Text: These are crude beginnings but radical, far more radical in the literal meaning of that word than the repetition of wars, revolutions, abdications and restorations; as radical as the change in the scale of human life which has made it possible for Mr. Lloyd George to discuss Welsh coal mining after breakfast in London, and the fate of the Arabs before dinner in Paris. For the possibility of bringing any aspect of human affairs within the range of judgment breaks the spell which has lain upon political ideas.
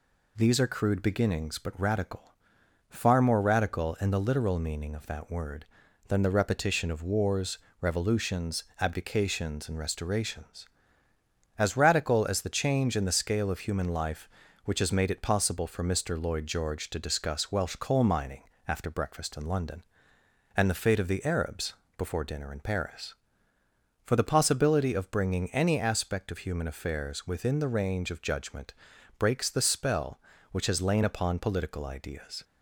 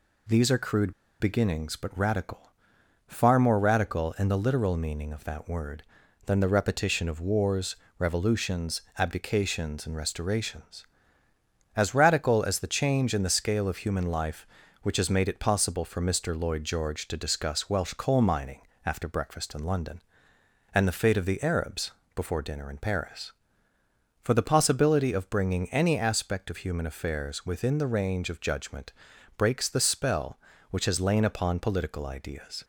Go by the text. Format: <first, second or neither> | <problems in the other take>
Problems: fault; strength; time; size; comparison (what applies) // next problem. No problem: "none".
first | pauses between "crude" and "beginnings"; slight; at 0.9 s; 0.28 s long // pauses between "mining" and "after"; slight; at 18.6 s; 0.26 s long; slight in the first // pauses between "Arabs" and "before"; slight; at 21.9 s; 0.24 s long; slight in the first // pauses between "judgment" and "breaks"; at 28.9 s; 0.44 s long; also in the first